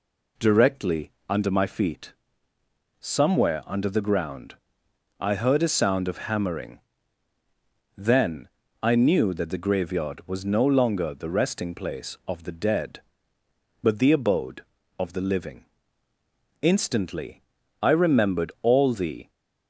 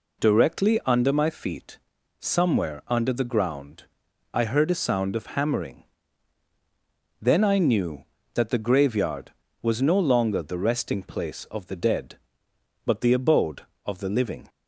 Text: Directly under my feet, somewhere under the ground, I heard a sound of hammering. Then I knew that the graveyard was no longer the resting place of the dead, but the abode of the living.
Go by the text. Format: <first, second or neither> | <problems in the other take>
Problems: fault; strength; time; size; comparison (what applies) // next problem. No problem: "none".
second | pauses between "Directly" and "under"; slight; at 1.1 s; 0.18 s long // pauses between "Then" and "I"; slight; at 8.4 s; 0.34 s long // goes on to say "Instantly I remembered all the"; strong; from 16.6 s on; 2.6 s long